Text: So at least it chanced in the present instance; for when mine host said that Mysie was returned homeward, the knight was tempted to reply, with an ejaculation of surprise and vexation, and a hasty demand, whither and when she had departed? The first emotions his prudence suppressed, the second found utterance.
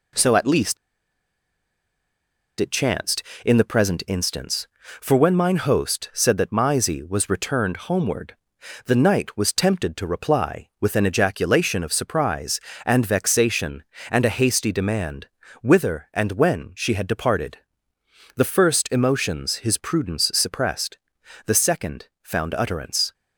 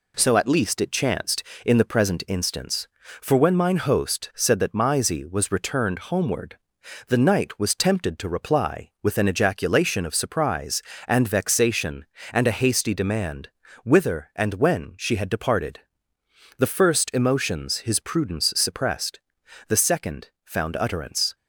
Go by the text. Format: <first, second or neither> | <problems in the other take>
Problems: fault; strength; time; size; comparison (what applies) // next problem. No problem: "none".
second | pauses between "least" and "it"; strong; at 0.7 s; 1.8 s long // pauses between "second" and "found"; slight; at 22.0 s; 0.16 s long; slight in the second